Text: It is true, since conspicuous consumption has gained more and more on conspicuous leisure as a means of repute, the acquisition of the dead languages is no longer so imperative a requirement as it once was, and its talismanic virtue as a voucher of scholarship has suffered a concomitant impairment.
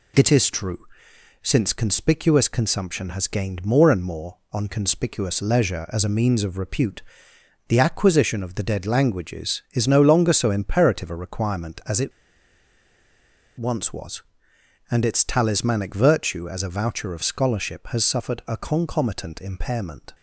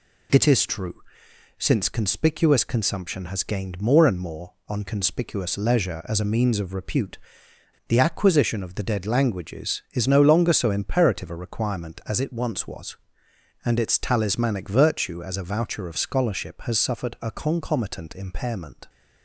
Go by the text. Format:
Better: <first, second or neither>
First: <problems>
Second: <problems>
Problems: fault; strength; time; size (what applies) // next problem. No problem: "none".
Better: second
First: pauses between "it" and "once"; strong; at 12.1 s; 1.4 s long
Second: none